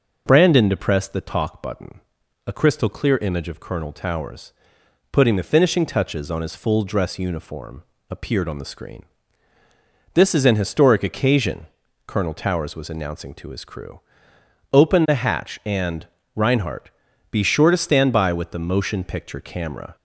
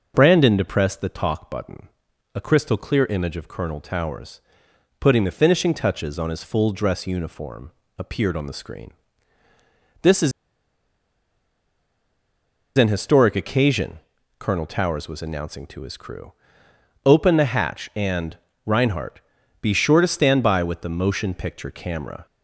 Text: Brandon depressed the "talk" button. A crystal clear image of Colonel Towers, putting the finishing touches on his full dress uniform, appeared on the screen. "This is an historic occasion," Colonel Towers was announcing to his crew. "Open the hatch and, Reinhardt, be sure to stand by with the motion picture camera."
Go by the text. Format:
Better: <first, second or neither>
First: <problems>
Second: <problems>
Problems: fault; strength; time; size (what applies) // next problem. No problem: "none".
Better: first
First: none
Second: pauses between "is" and "an"; strong; at 10.3 s; 2.4 s long